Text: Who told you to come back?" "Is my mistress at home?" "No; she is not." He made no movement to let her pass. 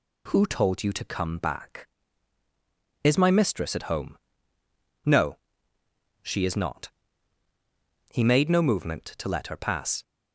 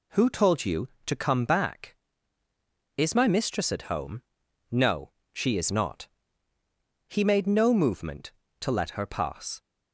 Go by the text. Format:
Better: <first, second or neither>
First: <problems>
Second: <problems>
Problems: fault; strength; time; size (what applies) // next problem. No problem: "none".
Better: neither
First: none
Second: none